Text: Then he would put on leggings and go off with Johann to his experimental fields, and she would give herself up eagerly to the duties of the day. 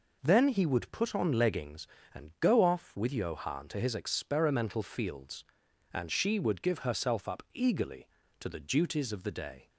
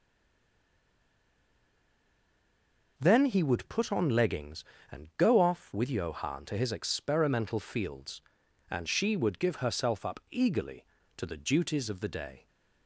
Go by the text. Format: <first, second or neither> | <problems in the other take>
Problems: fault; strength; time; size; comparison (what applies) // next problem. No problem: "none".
first | stays silent before the first word; strong; until 2.9 s; 2.9 s long